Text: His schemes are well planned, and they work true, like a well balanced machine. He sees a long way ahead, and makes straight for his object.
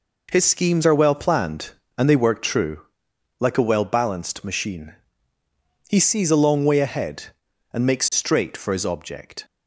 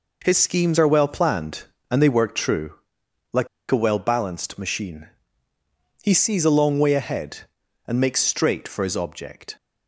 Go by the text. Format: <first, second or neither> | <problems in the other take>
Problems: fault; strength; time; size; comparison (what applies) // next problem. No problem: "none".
first | pauses between "like" and "a"; slight; at 3.4 s; 0.24 s long